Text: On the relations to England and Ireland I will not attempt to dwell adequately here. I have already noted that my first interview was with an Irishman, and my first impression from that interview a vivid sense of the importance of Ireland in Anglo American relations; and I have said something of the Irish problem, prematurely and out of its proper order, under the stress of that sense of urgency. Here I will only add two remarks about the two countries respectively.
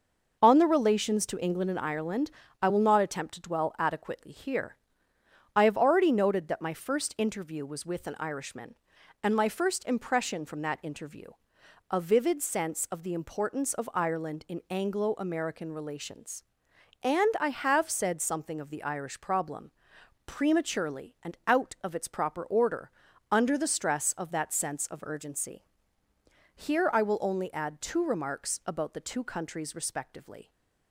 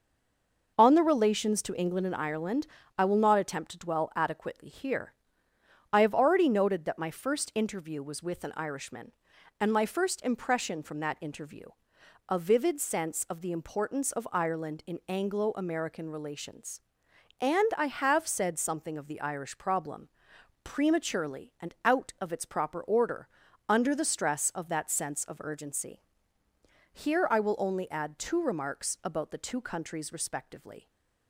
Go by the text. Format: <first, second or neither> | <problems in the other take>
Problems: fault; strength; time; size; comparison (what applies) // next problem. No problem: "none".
first | stays silent before the first word; slight; until 0.7 s; 0.7 s long // pauses between "Ireland" and "I"; slight; at 2.6 s; 0.32 s long; slight in the first // pauses between "interview" and "a"; noticeable; at 11.6 s; 0.62 s long; noticeable in the first // stays silent after the last word; slight; from 30.7 s on; 0.5 s long